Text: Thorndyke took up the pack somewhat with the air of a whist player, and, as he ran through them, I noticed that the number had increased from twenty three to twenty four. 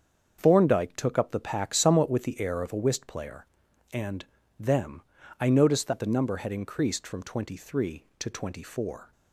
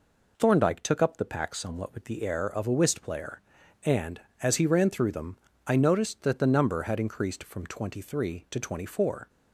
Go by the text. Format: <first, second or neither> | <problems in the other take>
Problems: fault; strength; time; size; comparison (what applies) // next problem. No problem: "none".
second | starts louder than the rest; until 1.4 s; 7 dB // skips "as he ran through"; at 4.4 s